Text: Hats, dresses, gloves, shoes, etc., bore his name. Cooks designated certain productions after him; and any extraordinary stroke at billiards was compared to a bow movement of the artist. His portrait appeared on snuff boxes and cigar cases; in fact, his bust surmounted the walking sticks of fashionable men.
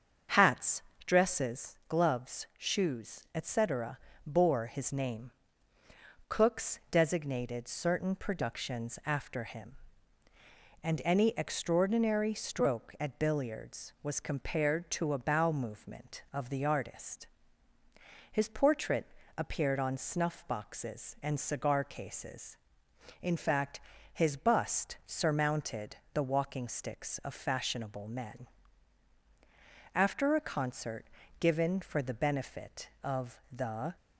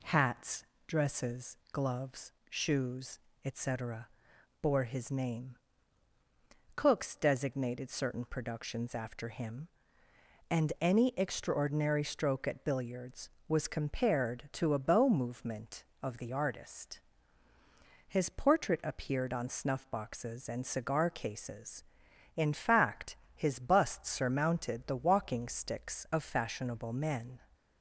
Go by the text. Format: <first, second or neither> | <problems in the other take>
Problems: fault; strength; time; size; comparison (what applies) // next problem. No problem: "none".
second | starts louder than the rest; until 1.6 s; 6.5 dB // pauses between "portrait" and "appeared"; slight; at 19.0 s; 0.28 s long // pauses between "surmounted" and "the"; slight; at 25.9 s; 0.18 s long // goes on to say "After a concert given for the benefit of the"; strong; from 29.9 s on; 4.0 s long